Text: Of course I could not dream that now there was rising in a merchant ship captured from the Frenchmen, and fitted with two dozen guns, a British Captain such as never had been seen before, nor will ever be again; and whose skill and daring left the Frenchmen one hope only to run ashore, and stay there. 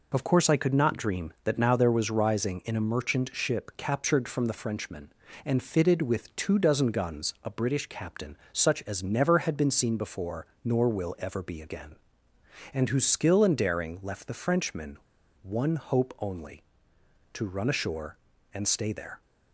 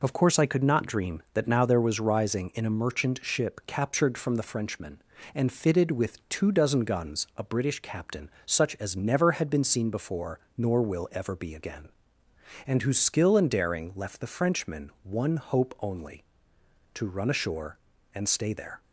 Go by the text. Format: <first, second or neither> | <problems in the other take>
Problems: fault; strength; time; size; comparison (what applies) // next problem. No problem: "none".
second | pauses between "Captain" and "such"; slight; at 8.3 s; 0.16 s long; slight in the second // pauses between "Frenchmen" and "one"; at 14.9 s; 0.42 s long